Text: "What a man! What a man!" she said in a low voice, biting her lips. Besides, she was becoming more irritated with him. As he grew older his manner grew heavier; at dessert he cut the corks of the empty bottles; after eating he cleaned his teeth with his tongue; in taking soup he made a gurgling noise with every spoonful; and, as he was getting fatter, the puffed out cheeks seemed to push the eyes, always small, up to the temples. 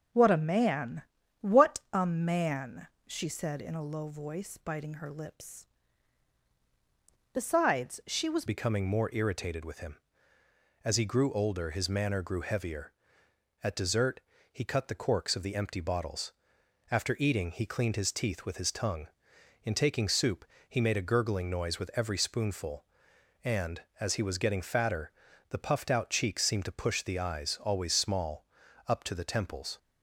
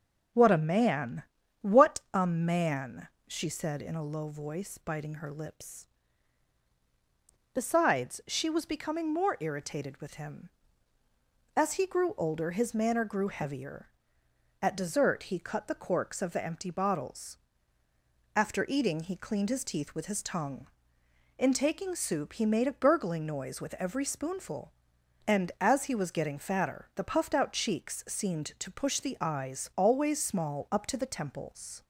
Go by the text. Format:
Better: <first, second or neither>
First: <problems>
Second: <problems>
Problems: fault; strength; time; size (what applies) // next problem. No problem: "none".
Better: second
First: changes voice at "becoming"; from 8.4 s on; 21.3 s long // pauses between "dessert" and "he"; slight; at 14.2 s; 0.30 s long // pauses between "soup" and "he"; slight; at 20.4 s; 0.28 s long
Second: none